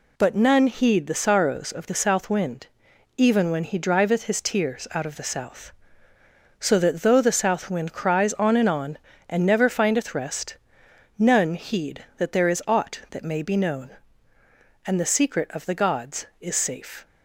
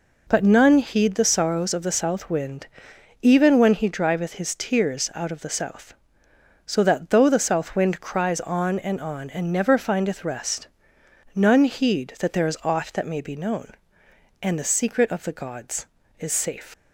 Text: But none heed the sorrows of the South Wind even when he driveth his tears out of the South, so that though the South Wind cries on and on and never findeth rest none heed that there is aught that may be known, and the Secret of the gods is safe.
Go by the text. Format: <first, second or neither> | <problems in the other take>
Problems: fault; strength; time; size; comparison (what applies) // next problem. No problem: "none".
first | pauses between "Wind" and "even"; noticeable; at 2.6 s; 0.54 s long; noticeable in the first // pauses between "rest" and "none"; noticeable; at 10.6 s; 0.66 s long; noticeable in the first // leaves "safe" unfinished; at 16.7 s; 110 ms